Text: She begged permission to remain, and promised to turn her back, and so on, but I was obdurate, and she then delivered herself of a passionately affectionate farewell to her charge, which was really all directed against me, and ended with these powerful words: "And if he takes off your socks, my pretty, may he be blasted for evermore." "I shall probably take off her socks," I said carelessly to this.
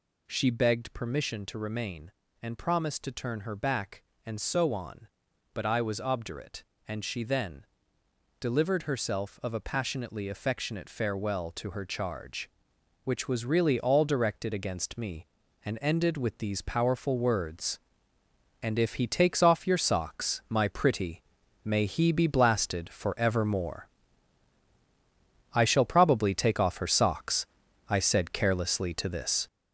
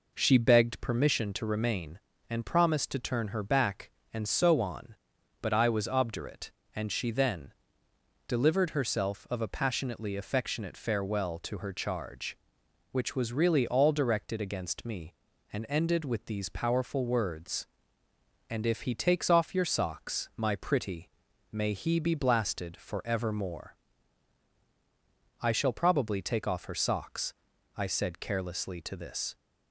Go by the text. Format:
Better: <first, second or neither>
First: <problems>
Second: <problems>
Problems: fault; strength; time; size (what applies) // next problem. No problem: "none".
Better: second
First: gets louder; throughout; 6.5 dB // pauses between "then" and "delivered"; noticeable; at 7.6 s; 0.74 s long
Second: pauses between "then" and "delivered"; noticeable; at 7.5 s; 0.74 s long